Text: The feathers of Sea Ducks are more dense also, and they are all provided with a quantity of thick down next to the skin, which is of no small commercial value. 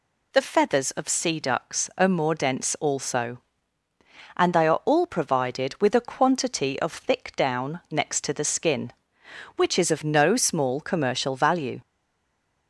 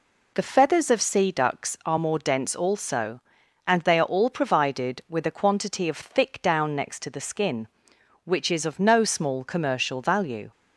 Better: second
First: stays silent after the last word; slight; from 11.8 s on; 0.8 s long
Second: none

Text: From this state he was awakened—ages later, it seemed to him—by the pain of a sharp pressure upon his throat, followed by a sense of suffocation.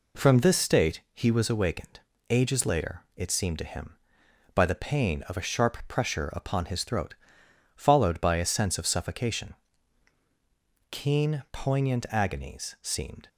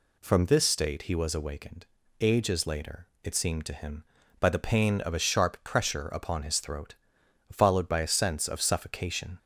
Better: second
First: goes on to say "Keen poignant agonies seemed"; strong; from 10.8 s on; 2.3 s long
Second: none

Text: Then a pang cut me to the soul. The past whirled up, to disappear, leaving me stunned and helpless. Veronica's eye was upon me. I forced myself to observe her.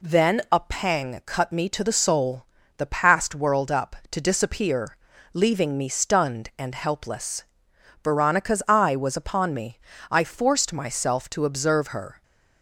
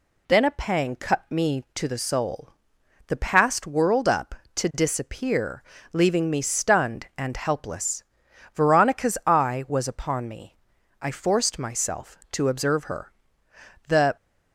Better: first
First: none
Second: goes on to say "The"; slight; from 13.8 s on; 0.28 s long

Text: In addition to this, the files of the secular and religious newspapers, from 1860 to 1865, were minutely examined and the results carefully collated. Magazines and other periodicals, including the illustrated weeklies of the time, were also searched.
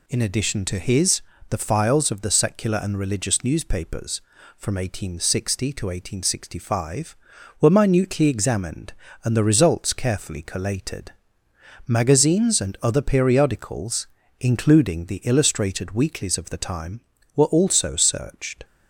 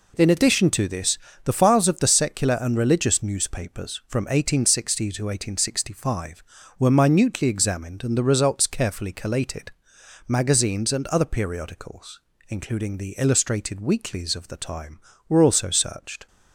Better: second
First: says "his" for "this"; at 0.7 s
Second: none

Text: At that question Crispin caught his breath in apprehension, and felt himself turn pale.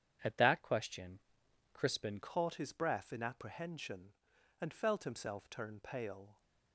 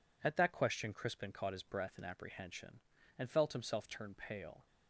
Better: second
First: starts louder than the rest; strong; until 1.7 s; 8.5 dB // pauses between "question" and "Crispin"; noticeable; at 1.2 s; 0.52 s long // changes voice at "caught"; from 2.2 s on; 4.2 s long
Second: none

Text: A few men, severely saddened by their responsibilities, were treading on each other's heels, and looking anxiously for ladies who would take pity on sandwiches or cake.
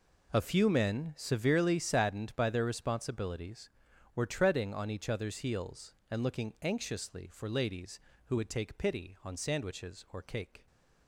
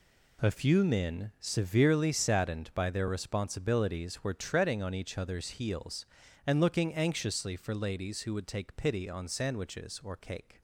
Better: neither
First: none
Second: none

